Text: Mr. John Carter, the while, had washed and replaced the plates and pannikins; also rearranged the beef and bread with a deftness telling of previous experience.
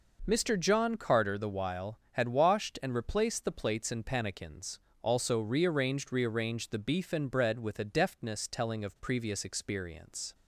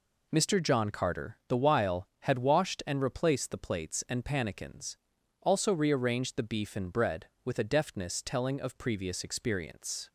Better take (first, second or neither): second